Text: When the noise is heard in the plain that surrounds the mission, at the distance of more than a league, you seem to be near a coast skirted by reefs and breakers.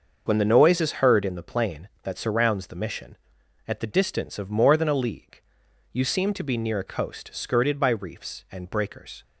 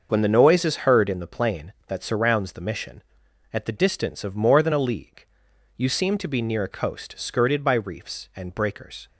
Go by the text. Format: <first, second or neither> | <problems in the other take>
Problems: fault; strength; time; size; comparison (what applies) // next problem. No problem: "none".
neither | starts louder than the rest; the same in both